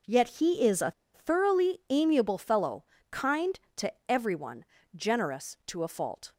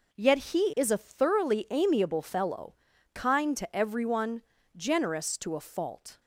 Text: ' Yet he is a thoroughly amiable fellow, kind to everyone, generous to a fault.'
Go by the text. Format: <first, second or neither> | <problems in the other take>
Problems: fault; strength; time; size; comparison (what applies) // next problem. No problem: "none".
second | pauses between "a" and "thoroughly"; slight; at 0.9 s; 0.23 s long // pauses between "to" and "everyone"; slight; at 3.9 s; 0.16 s long